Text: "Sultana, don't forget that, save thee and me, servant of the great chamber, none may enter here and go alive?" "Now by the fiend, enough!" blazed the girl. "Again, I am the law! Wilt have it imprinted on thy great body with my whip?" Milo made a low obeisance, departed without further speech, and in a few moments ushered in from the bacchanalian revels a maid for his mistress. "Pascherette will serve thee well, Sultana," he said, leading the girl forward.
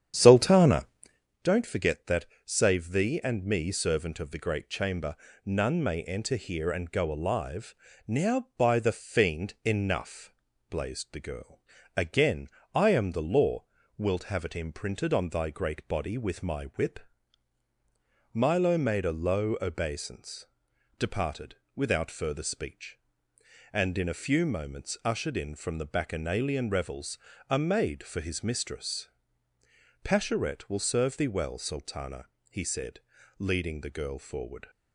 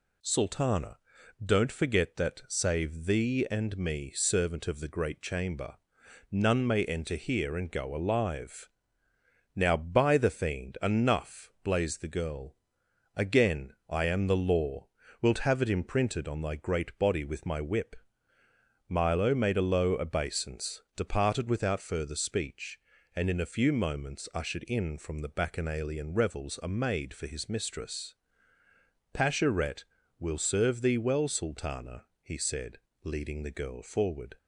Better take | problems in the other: second | starts louder than the rest; strong; until 1.4 s; 9.5 dB // pauses between "departed" and "without"; slight; at 21.5 s; 0.18 s long // pauses between "revels" and "a"; slight; at 27.1 s; 0.30 s long

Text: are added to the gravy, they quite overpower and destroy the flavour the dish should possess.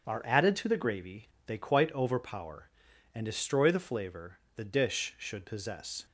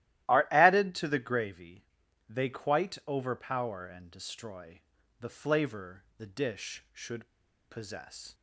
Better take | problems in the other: first | starts louder than the rest; strong; until 1.3 s; 14.5 dB; strong in the first // pauses between "destroy" and "the"; at 4.7 s; 0.40 s long // pauses between "flavour" and "the"; slight; at 6.0 s; 0.16 s long; slight in the first // pauses between "should" and "possess"; at 7.2 s; 0.42 s long

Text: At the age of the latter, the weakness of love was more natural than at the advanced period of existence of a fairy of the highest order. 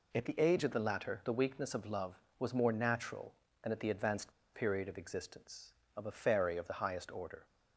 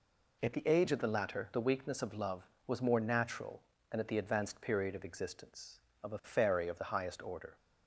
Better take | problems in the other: second | pauses between "advanced" and "period"; slight; at 4.3 s; 0.21 s long

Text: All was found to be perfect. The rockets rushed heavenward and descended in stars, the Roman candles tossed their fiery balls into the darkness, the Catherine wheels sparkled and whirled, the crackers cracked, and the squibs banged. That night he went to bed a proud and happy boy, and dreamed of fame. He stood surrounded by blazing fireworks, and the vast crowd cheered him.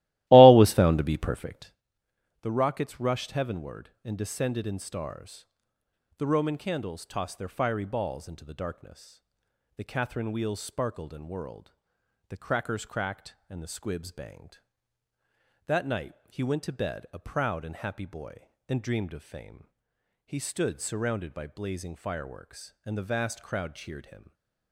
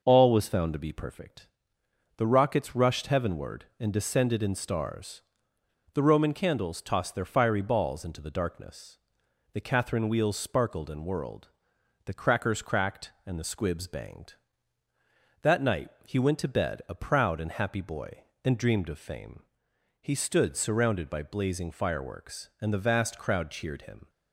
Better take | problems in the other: second | starts louder than the rest; strong; until 1.8 s; 16.5 dB // pauses between "night" and "he"; slight; at 16.1 s; 0.16 s long; slight in the second // stays silent after the last word; slight; from 24.1 s on; 0.6 s long

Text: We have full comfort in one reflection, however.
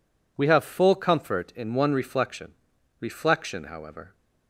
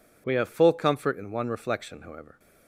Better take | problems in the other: second | says "reflection" twice; at 3.0 s

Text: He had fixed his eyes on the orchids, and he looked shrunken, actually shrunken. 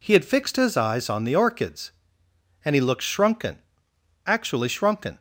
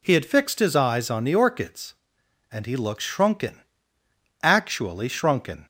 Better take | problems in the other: neither | none

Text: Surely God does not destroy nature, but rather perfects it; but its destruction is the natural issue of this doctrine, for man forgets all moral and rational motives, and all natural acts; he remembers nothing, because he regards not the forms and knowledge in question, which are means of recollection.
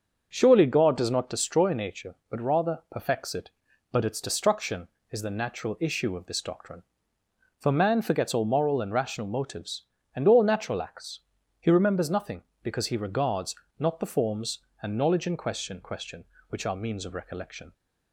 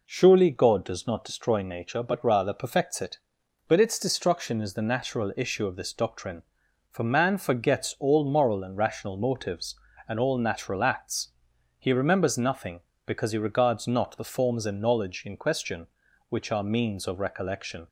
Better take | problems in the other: second | starts louder than the rest; until 1.3 s; 6.5 dB // pauses between "regards" and "not"; slight; at 13.5 s; 0.20 s long // says "question" twice; at 15.8 s

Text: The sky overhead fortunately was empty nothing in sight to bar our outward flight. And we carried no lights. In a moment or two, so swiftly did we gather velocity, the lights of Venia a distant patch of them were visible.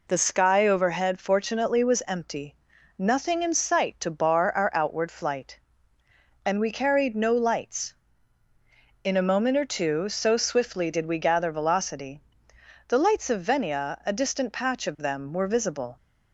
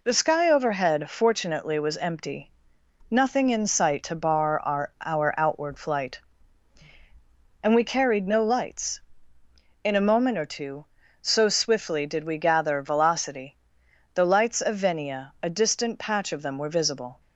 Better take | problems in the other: first | pauses between "empty" and "nothing"; noticeable; at 2.5 s; 0.60 s long; also in the first // says "our" twice; at 5.0 s

